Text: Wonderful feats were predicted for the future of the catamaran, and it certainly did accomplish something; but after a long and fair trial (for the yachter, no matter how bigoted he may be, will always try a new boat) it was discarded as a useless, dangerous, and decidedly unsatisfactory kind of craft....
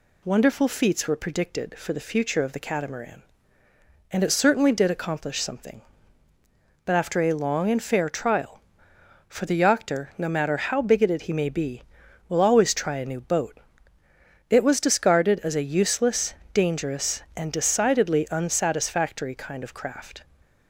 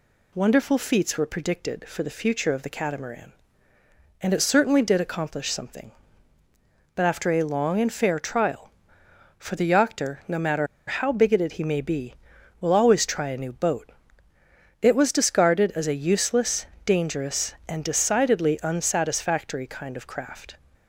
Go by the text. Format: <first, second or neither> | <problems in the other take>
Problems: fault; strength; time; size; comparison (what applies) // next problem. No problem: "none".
first | pauses between "matter" and "how"; slight; at 10.6 s; 0.22 s long